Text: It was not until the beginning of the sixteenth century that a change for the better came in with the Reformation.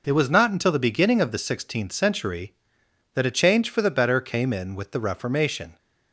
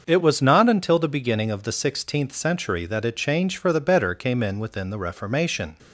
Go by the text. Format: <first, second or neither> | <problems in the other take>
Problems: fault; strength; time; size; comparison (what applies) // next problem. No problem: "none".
first | starts louder than the rest; until 1.0 s; 6.5 dB // says "within" for "with"; at 4.5 s